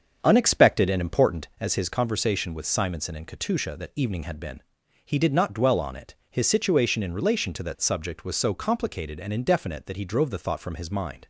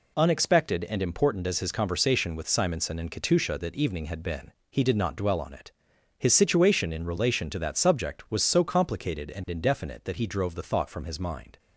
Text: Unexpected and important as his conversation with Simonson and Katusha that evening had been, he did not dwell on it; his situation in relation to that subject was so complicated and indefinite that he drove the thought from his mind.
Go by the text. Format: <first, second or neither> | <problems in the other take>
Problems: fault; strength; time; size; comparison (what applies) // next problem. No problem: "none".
second | starts louder than the rest; until 1.5 s; 7 dB